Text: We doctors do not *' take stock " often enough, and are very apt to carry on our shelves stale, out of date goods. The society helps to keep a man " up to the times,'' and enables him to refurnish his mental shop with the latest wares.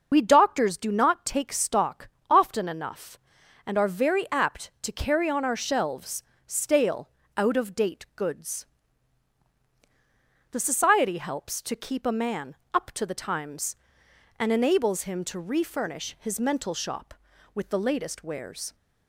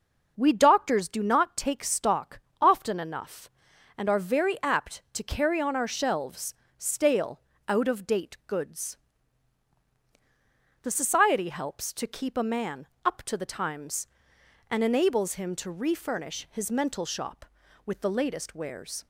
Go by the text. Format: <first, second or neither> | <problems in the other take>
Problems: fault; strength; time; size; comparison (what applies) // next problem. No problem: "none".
second | loses the start of "We"; at 0.1 s; 70 ms // pauses between "shelves" and "stale"; slight; at 6.2 s; 0.24 s long; slight in the second